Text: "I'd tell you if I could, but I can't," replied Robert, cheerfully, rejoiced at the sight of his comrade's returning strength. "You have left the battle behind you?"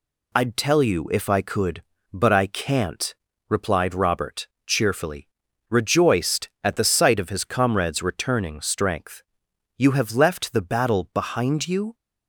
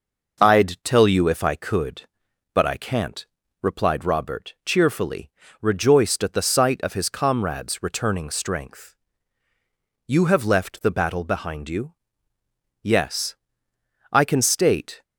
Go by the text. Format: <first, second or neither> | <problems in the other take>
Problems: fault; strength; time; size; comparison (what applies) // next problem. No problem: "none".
first | goes on to say "Yes I can state"; strong; from 12.8 s on; 2.1 s long